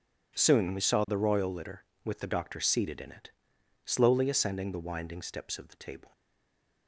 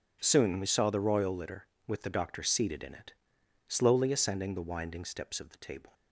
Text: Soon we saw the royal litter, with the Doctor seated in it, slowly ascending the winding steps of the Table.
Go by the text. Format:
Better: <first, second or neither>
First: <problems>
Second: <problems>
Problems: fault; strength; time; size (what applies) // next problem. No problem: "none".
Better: second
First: stays silent after the last word; slight; from 6.1 s on; 0.7 s long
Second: none